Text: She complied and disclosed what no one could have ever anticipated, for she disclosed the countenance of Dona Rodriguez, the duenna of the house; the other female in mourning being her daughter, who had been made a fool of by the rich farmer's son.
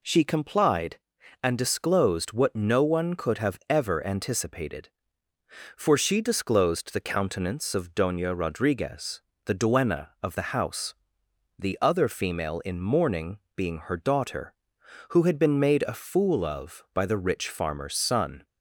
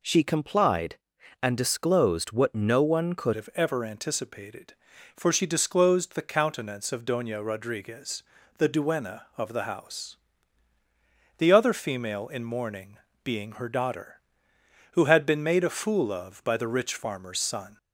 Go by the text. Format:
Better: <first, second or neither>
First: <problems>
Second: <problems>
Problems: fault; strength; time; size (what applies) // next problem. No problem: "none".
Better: first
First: pauses between "mourning" and "being"; slight; at 13.3 s; 0.16 s long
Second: changes voice at "have"; from 3.3 s on; 14.4 s long // pauses between "mourning" and "being"; slight; at 12.9 s; 0.26 s long